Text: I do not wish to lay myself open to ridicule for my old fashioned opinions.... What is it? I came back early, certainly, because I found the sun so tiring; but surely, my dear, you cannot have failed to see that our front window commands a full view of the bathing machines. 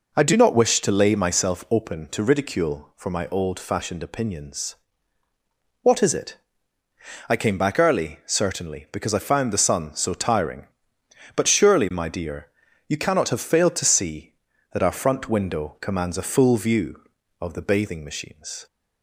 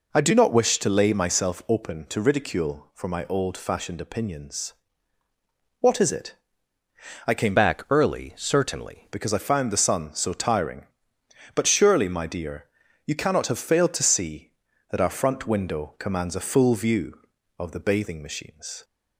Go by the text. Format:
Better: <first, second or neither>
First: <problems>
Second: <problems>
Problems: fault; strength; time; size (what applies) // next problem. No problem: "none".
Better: first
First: none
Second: changes voice from "back" to "certainly"; from 7.5 to 9.0 s; 1.5 s long